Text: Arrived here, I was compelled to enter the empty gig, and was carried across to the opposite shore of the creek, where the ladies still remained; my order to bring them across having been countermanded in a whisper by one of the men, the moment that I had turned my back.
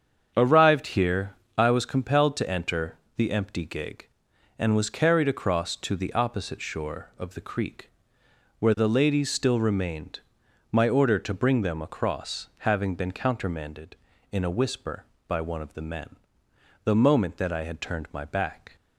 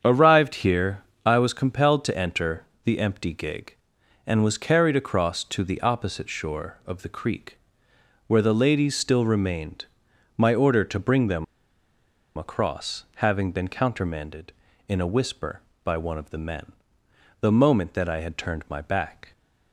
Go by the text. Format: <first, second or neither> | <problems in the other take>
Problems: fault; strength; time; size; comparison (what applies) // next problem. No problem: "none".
first | starts louder than the rest; strong; until 1.0 s; 7.5 dB; strong in the first // pauses between "enter" and "the"; slight; at 2.6 s; 0.20 s long; slight in the first // pauses between "them" and "across"; noticeable; at 11.4 s; 0.93 s long // pauses between "across" and "having"; slight; at 13.0 s; 0.18 s long; slight in the first